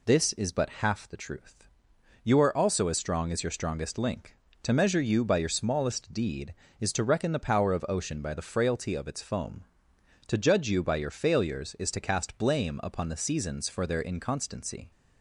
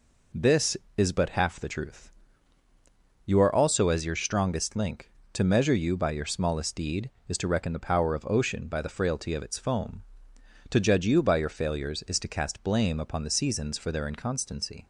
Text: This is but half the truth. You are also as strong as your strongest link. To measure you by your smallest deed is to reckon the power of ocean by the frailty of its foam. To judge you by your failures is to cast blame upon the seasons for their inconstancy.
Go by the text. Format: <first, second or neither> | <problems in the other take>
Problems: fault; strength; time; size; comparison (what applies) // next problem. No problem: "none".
first | skips "as strong"; at 3.8 s